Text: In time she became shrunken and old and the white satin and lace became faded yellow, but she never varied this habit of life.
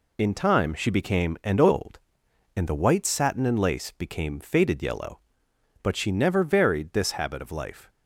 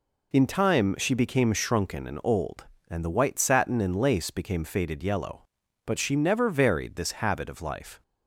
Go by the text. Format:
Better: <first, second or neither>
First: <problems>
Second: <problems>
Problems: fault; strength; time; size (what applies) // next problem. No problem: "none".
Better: second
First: skips "shrunken"; at 1.4 s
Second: none